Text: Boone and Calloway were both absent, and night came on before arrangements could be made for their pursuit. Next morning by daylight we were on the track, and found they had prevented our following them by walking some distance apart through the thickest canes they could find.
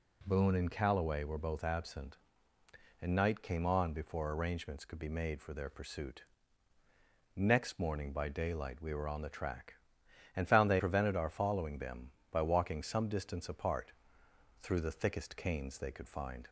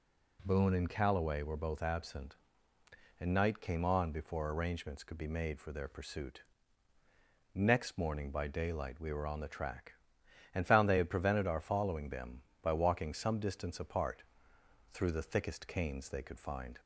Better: second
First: skips "had"; at 10.7 s // pauses between "apart" and "through"; noticeable; at 13.9 s; 0.68 s long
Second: pauses between "apart" and "through"; noticeable; at 14.2 s; 0.68 s long

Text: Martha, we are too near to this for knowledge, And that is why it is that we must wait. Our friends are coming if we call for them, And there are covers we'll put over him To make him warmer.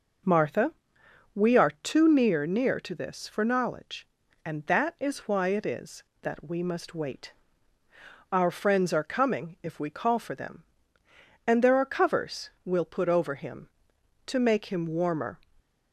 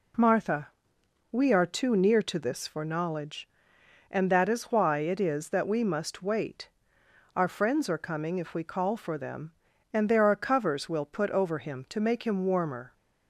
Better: second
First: says "near" twice; at 2.4 s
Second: none

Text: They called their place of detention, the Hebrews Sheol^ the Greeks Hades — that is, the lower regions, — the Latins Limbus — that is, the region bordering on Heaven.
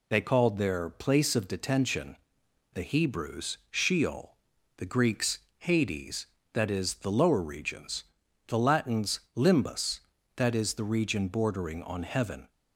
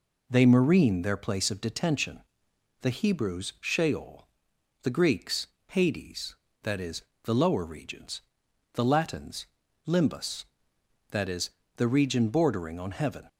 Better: first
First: pauses between "Sheol" and "the"; at 4.3 s; 0.44 s long // pauses between "Greeks" and "Hades"; slight; at 5.3 s; 0.20 s long // pauses between "Latins" and "Limbus"; slight; at 9.2 s; 0.16 s long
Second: says "marine" for "called"; at 0.4 s // pauses between "Sheol" and "the"; noticeable; at 4.2 s; 0.58 s long // pauses between "Greeks" and "Hades"; slight; at 5.4 s; 0.22 s long // pauses between "Latins" and "Limbus"; at 9.4 s; 0.40 s long

